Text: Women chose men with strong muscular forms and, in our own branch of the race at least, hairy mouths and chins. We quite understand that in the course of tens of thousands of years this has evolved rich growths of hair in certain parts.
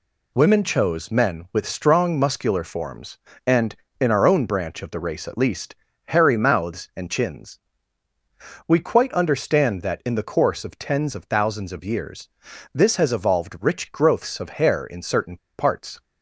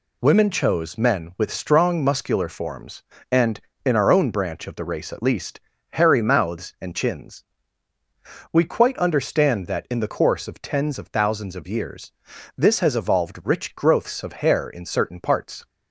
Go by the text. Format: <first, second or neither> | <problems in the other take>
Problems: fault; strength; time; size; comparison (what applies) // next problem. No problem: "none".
second | pauses between "years" and "this"; at 12.2 s; 0.44 s long; also in the second // pauses between "certain" and "parts"; slight; at 15.3 s; 0.20 s long